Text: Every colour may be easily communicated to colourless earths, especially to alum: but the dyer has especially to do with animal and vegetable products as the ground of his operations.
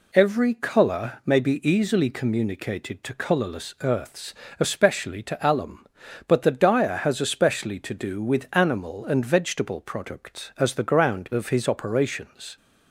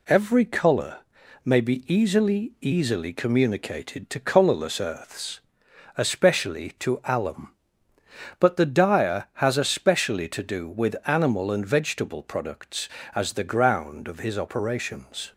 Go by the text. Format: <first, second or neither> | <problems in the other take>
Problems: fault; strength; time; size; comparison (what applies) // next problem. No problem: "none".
first | pauses between "colour" and "may"; at 1.0 s; 0.44 s long // says "easily" twice; at 2.5 s